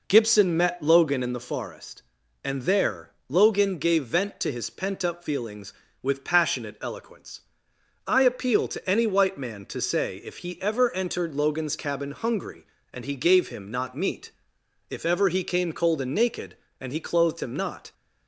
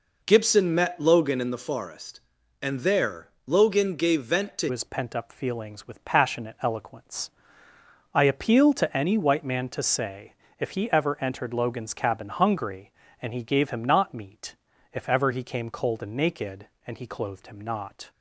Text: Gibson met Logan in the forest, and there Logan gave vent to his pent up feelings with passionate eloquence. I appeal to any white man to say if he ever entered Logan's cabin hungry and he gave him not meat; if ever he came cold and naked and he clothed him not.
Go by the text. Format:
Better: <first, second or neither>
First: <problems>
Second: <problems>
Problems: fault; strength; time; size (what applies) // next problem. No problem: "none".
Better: first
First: pauses between "there" and "Logan"; slight; at 3.1 s; 0.20 s long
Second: pauses between "there" and "Logan"; slight; at 3.2 s; 0.20 s long // changes voice at "his"; from 4.6 s on; 13.4 s long // pauses between "say" and "if"; slight; at 10.3 s; 0.26 s long